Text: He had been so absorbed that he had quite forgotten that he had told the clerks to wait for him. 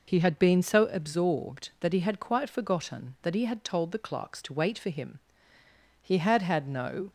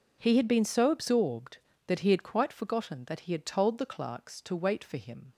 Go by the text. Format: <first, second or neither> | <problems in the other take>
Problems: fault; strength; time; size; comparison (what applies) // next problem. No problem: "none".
second | goes on to say "He had had no"; noticeable; from 6.0 s on; 1.0 s long